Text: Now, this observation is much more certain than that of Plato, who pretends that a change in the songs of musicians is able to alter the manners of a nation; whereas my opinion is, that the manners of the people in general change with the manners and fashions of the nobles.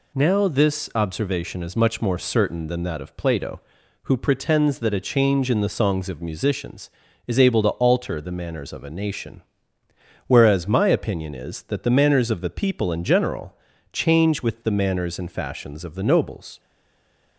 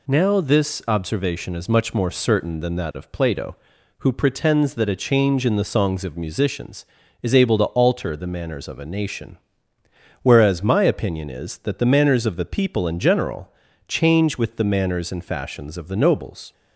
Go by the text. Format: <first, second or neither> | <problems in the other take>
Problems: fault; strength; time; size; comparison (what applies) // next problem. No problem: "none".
second | pauses between "general" and "change"; at 13.5 s; 0.38 s long; also in the second // stays silent after the last word; slight; from 16.5 s on; 0.8 s long